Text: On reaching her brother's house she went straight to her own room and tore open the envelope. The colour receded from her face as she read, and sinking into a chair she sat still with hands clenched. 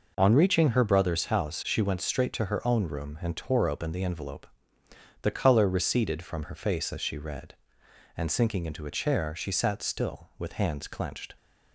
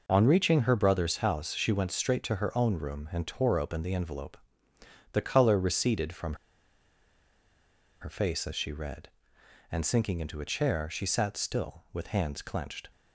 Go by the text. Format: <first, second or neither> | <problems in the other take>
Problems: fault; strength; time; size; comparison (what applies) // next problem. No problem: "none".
first | pauses between "from" and "her"; strong; at 6.3 s; 1.6 s long